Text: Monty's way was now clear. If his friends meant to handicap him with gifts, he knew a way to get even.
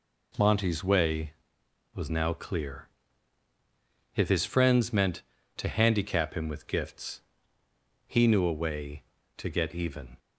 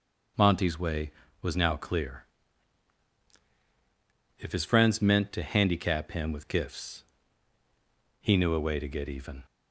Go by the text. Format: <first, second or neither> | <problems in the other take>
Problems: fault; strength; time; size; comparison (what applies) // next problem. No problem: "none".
neither | none